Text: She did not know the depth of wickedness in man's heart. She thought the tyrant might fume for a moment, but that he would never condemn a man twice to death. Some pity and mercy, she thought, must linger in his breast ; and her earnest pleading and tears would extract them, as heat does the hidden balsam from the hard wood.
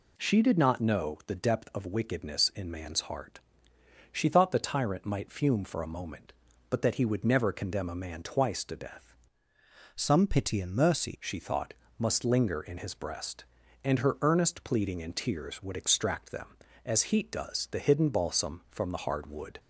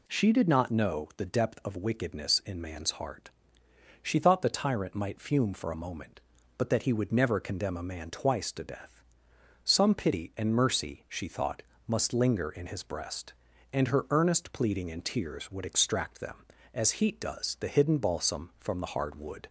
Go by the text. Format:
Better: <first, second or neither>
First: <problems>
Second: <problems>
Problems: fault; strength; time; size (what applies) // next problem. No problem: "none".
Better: second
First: changes voice from "Some" to "mercy"; from 9.9 to 11.1 s; 1.2 s long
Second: none